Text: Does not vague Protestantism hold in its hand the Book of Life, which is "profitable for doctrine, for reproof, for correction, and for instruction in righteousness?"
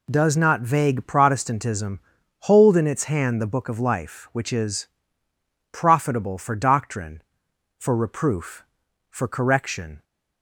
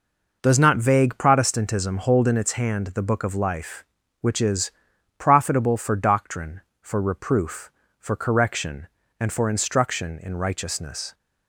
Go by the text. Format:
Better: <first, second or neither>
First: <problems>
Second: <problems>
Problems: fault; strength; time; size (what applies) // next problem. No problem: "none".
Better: second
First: pauses between "Protestantism" and "hold"; at 1.9 s; 0.42 s long // pauses between "is" and "profitable"; noticeable; at 4.8 s; 0.84 s long // stops before "and for instruction in righteousness"; at 10.0 s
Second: pauses between "is" and "profitable"; noticeable; at 4.7 s; 0.46 s long